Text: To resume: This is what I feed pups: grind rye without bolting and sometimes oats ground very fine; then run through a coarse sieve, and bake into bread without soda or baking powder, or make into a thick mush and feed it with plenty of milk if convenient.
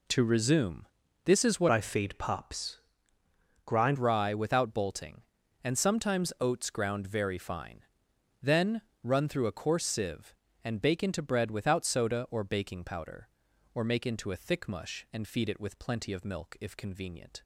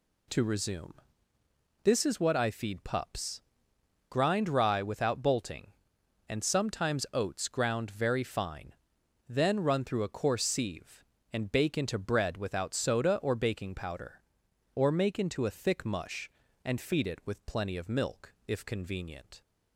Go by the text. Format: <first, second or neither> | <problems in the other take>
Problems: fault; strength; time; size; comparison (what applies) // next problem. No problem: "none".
second | changes voice from "I" to "grind"; from 1.7 to 3.9 s; 2.2 s long // pauses between "then" and "run"; slight; at 8.8 s; 0.20 s long